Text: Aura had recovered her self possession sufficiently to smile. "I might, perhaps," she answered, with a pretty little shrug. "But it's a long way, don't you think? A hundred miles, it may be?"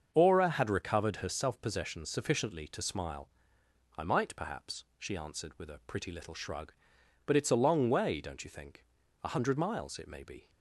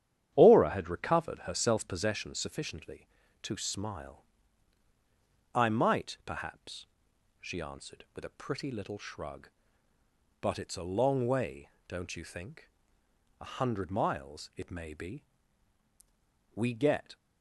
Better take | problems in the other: first | starts louder than the rest; strong; until 1.3 s; 10 dB; also in the first // goes on to say "We get"; noticeable; from 16.5 s on; 0.62 s long

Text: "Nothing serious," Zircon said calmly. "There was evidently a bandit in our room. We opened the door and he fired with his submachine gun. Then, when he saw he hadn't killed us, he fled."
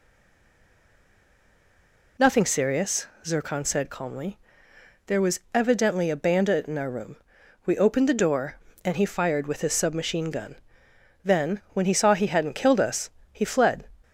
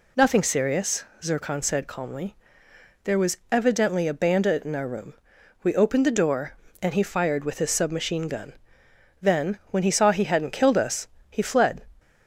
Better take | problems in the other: second | stays silent before the first word; until 2.1 s; 2.1 s long

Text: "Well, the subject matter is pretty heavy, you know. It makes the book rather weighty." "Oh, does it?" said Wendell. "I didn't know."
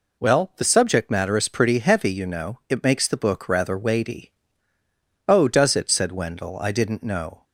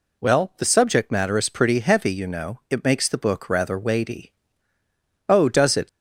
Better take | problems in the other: first | stops before "said Wendell I didn't know"; at 5.8 s

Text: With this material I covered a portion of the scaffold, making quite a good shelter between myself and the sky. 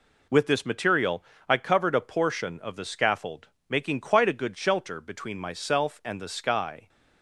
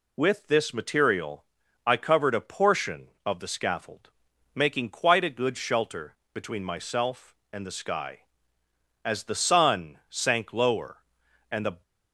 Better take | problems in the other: first | pauses between "material" and "I"; at 1.4 s; 0.42 s long; slight in the first // pauses between "shelter" and "between"; slight; at 6.1 s; 0.20 s long // goes on to say "As the sun sank lower and the"; strong; from 9.0 s on; 2.7 s long

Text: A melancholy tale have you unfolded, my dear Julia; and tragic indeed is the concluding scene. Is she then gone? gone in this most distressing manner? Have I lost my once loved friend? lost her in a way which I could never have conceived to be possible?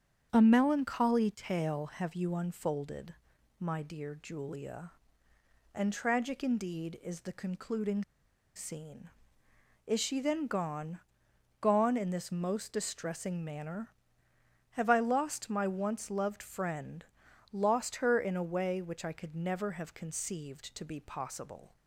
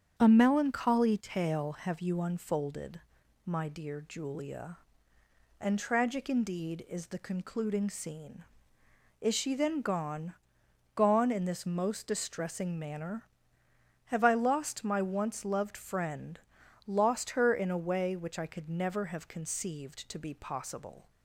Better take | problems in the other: second | starts louder than the rest; strong; until 1.3 s; 8 dB; strong in the second // pauses between "concluding" and "scene"; noticeable; at 8.0 s; 0.51 s long

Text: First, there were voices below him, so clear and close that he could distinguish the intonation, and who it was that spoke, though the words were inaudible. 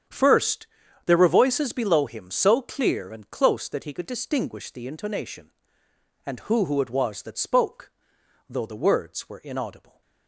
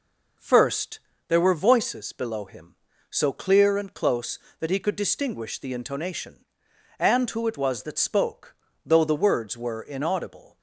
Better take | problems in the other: second | starts louder than the rest; strong; until 1.4 s; 8.5 dB // says "who" twice; at 6.6 s

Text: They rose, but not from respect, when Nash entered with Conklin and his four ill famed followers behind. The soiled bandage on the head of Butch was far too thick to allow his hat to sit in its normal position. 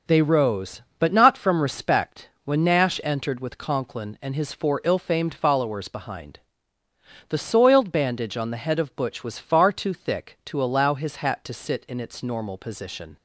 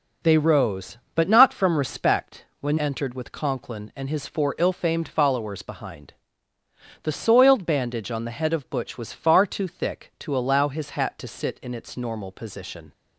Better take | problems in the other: first | skips "Nash"; at 2.7 s

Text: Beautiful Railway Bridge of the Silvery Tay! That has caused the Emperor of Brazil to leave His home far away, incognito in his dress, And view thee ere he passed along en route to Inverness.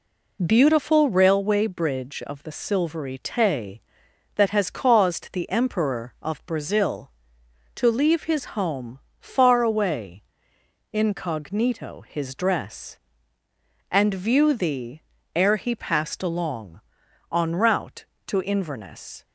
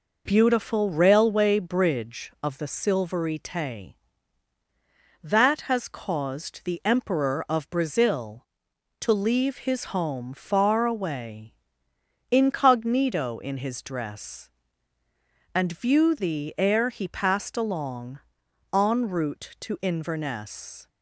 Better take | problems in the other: second | pauses between "home" and "far"; slight; at 9.0 s; 0.20 s long // skips "in"; at 12.0 s // pauses between "thee" and "ere"; slight; at 15.0 s; 0.34 s long // pauses between "along" and "en"; noticeable; at 16.8 s; 0.50 s long; noticeable in the second

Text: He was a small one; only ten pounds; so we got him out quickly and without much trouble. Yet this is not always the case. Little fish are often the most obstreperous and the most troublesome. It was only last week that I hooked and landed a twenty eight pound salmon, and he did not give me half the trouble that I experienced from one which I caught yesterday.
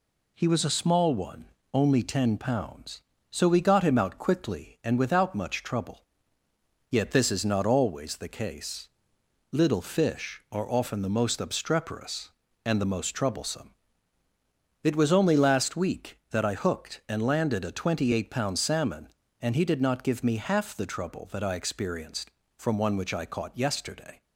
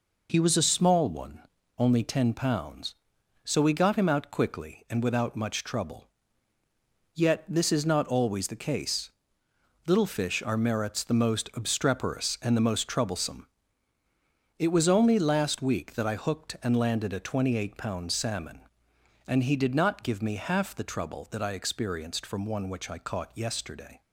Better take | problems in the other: first | says "merits" for "often"; at 10.5 s

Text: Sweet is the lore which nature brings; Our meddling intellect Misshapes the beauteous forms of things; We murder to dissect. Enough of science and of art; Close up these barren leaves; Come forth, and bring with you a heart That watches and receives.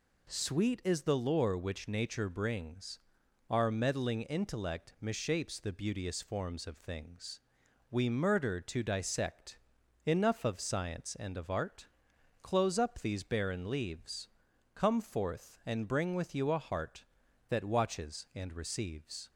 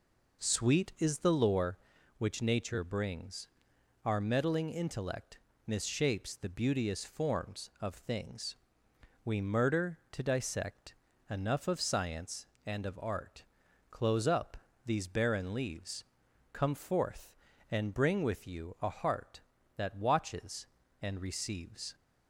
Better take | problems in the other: first | starts louder than the rest; noticeable; until 1.7 s; 4.5 dB // pauses between "intellect" and "Misshapes"; slight; at 5.3 s; 0.28 s long // pauses between "up" and "these"; slight; at 14.6 s; 0.20 s long

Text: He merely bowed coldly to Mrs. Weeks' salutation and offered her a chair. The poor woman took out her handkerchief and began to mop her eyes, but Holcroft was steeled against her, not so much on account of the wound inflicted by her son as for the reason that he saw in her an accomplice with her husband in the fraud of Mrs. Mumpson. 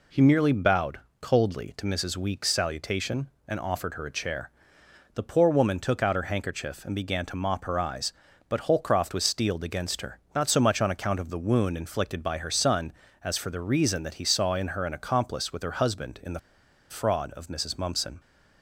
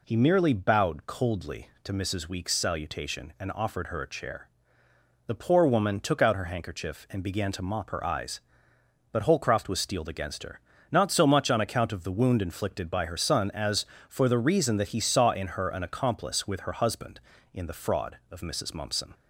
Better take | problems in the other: second | pauses between "bowed" and "coldly"; slight; at 0.9 s; 0.22 s long // pauses between "the" and "fraud"; noticeable; at 16.3 s; 0.50 s long

